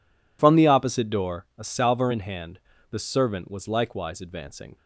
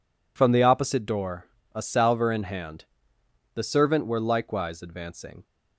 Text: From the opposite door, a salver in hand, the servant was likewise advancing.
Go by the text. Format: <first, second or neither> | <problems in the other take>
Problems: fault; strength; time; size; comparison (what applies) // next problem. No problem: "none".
first | says "were" for "was"; at 4.0 s